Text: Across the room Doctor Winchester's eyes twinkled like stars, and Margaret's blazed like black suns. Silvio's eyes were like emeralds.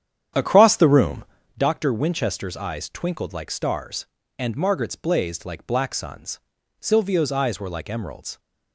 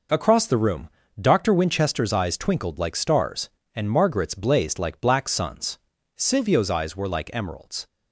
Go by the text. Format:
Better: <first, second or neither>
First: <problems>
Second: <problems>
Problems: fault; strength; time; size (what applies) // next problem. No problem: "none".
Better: second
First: starts louder than the rest; strong; until 1.6 s; 9.5 dB // pauses between "room" and "Doctor"; slight; at 1.2 s; 0.34 s long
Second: pauses between "room" and "Doctor"; slight; at 0.8 s; 0.32 s long